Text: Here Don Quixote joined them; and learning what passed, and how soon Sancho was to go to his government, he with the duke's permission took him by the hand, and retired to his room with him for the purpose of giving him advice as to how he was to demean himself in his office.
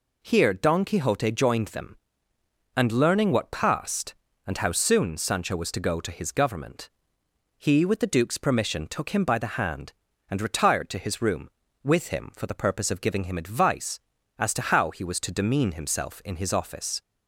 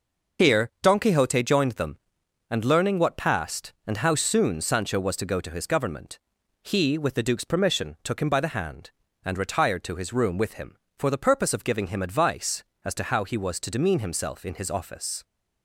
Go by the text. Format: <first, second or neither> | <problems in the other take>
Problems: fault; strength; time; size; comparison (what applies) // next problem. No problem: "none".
first | loses the start of "Here"; at 0.3 s; 45 ms // starts louder than the rest; noticeable; until 1.5 s; 6 dB